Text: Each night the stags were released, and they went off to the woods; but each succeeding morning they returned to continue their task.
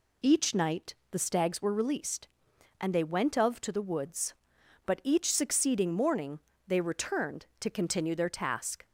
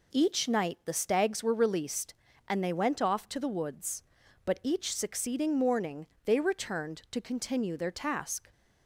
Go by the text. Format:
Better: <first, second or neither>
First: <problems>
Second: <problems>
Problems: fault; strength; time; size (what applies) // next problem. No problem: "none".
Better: second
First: pauses between "night" and "the"; slight; at 0.9 s; 0.16 s long // says "of" for "off"; at 3.3 s // pauses between "morning" and "they"; slight; at 6.3 s; 0.30 s long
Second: pauses between "morning" and "they"; slight; at 6.0 s; 0.20 s long